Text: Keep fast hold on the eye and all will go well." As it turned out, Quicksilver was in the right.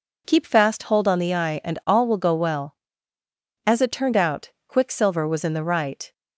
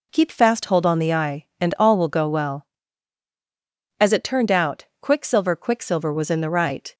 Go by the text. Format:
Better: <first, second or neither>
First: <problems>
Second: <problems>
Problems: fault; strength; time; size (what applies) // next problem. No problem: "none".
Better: first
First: none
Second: says "Quicksilver" twice; at 5.5 s